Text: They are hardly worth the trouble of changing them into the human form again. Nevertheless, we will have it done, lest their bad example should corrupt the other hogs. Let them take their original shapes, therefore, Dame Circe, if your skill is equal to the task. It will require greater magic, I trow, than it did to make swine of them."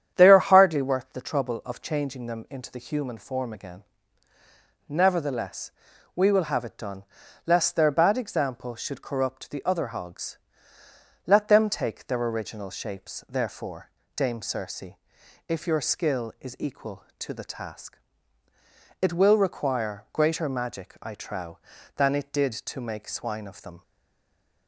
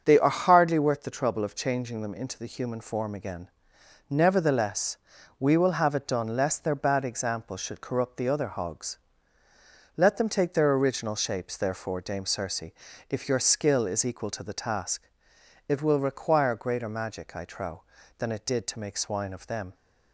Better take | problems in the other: second | starts louder than the rest; strong; until 1.1 s; 9 dB; also in the second // stays silent after the last word; slight; from 23.8 s on; 0.8 s long

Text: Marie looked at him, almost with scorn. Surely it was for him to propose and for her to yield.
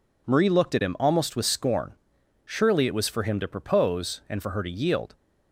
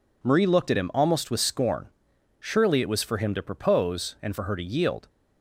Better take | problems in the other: neither | none

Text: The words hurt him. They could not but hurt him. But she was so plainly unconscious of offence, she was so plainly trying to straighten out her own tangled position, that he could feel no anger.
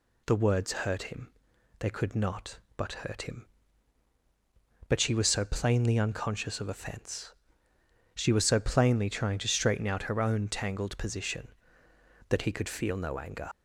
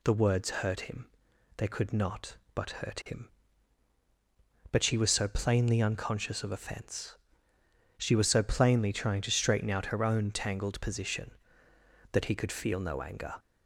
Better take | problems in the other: second | leaves "anger" unfinished; at 13.5 s; 40 ms

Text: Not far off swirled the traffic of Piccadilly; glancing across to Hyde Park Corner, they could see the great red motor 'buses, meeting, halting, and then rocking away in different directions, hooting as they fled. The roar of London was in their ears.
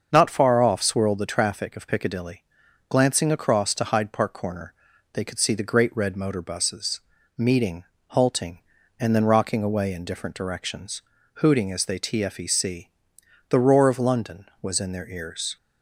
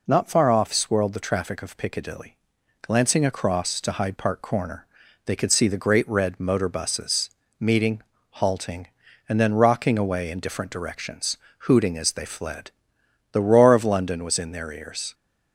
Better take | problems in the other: second | starts louder than the rest; until 1.1 s; 6.5 dB // says "tfec" for "fled"; at 11.9 s

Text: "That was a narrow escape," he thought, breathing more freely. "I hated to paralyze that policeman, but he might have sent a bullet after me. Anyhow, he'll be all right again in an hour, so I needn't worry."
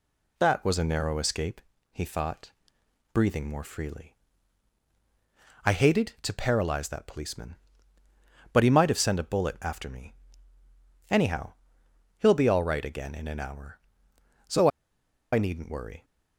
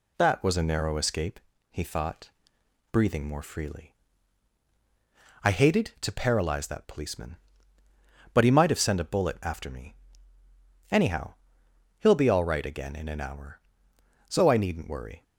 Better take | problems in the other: second | pauses between "so" and "I"; noticeable; at 14.6 s; 0.64 s long

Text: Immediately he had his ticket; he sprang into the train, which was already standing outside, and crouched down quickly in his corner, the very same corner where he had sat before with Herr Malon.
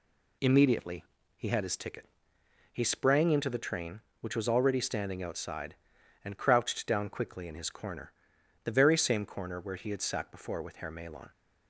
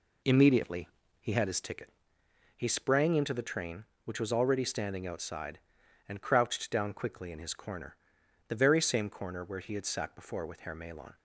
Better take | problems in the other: first | starts louder than the rest; slight; until 1.8 s; 3 dB // pauses between "Immediately" and "he"; slight; at 0.8 s; 0.34 s long; slight in the first

